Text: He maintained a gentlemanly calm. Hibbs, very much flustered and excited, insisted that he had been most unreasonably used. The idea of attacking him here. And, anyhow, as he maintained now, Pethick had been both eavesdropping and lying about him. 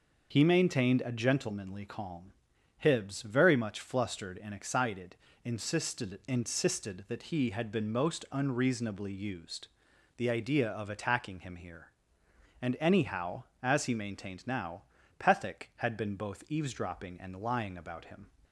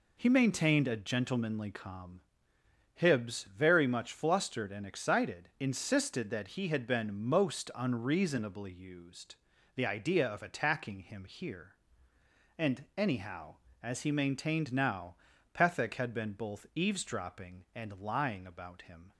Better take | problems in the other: second | starts louder than the rest; noticeable; until 1.3 s; 6 dB // says "insisted" twice; at 6.2 s

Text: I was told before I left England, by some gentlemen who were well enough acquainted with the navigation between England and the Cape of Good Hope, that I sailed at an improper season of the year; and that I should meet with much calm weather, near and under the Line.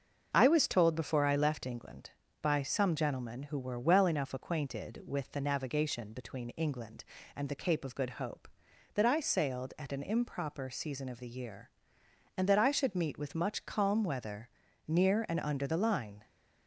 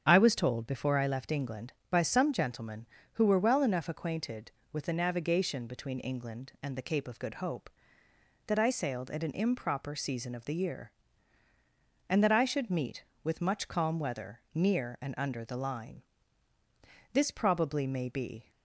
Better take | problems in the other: first | starts louder than the rest; strong; until 1.0 s; 8 dB; also in the first // goes on to say "This probably may be"; from 17.1 s on; 1.3 s long

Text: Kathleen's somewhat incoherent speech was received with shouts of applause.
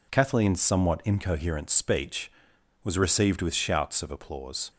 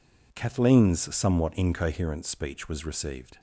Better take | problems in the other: first | stops before "with shouts of applause"; at 3.3 s

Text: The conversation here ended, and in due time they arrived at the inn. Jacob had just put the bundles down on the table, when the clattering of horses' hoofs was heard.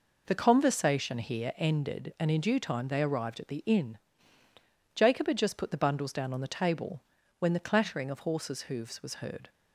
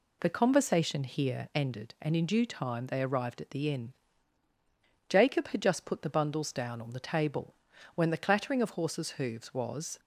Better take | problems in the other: first | stops before "heard"; at 9.9 s

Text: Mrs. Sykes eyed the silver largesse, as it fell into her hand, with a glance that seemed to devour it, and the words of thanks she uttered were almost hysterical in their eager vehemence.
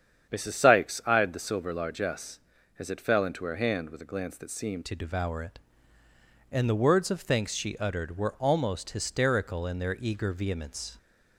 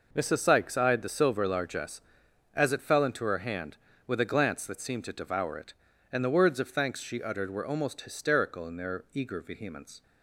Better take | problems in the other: second | starts louder than the rest; strong; until 1.3 s; 8.5 dB // changes voice at "to"; from 4.8 s on; 6.1 s long

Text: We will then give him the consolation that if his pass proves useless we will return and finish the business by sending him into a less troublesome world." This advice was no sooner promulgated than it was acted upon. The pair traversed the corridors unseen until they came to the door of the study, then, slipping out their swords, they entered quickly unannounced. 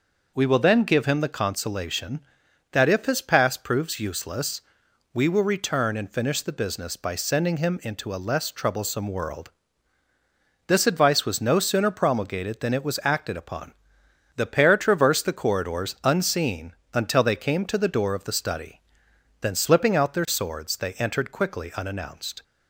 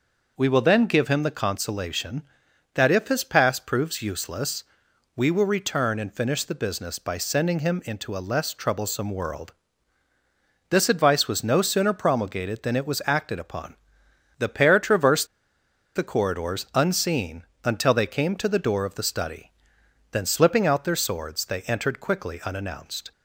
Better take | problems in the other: first | pauses between "useless" and "we"; noticeable; at 4.6 s; 0.54 s long; noticeable in the first // pauses between "traversed" and "the"; noticeable; at 15.2 s; 0.68 s long // pauses between "unseen" and "until"; slight; at 17.4 s; 0.20 s long; slight in the first

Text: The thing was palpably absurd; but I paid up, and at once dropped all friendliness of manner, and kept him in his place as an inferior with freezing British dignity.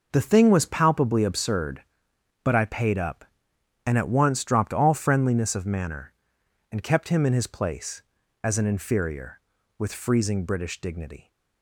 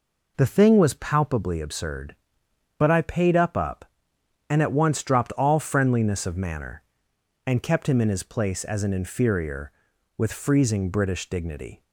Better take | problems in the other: first | says "up" twice; at 3.5 s

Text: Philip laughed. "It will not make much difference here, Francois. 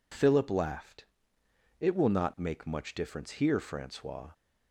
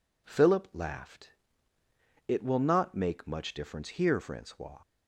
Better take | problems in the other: neither | none

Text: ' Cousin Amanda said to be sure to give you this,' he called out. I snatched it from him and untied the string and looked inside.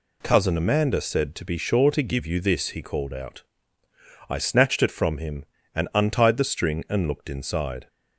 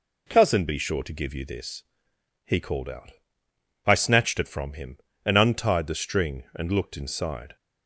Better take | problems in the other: first | skips "Amanda said to"; at 0.6 s

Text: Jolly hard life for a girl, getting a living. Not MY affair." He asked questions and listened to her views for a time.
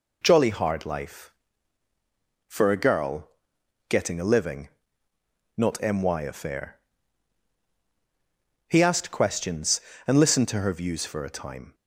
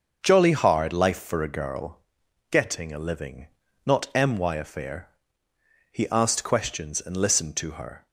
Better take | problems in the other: first | starts louder than the rest; until 1.2 s; 6 dB // stops before "views for a time"; at 8.0 s

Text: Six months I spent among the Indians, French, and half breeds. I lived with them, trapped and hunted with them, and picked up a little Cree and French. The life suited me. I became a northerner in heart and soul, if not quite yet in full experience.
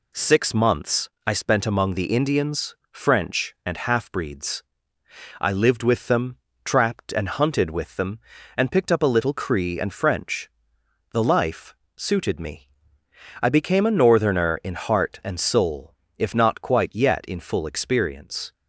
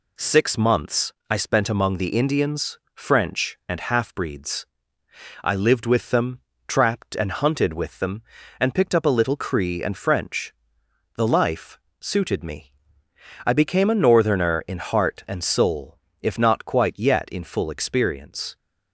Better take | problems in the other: neither | pauses between "months" and "I"; slight; the same in both // pauses between "life" and "suited"; slight; the same in both

